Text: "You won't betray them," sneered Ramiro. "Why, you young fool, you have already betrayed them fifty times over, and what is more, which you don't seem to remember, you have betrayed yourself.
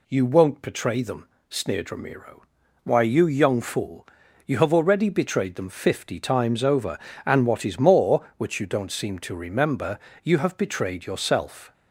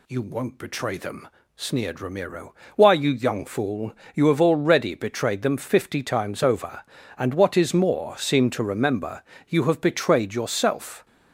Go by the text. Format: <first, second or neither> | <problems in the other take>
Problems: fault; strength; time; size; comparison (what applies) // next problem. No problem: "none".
first | skips "which you don't"; at 8.1 s